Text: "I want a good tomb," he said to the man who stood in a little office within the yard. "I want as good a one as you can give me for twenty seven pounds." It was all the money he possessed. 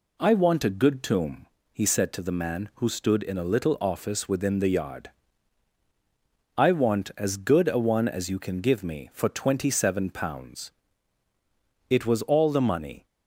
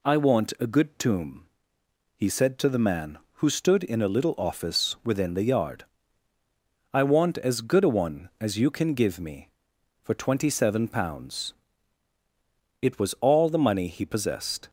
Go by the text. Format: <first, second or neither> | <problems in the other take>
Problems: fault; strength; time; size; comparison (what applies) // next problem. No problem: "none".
second | stops before "he possessed"; at 13.0 s